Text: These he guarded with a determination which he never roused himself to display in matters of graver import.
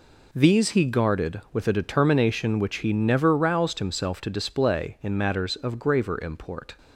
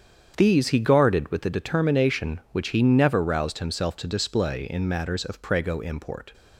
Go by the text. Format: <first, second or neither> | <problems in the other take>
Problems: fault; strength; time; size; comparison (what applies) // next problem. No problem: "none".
first | starts louder than the rest; strong; until 1.3 s; 8 dB // says "prego" for "graver"; at 5.4 s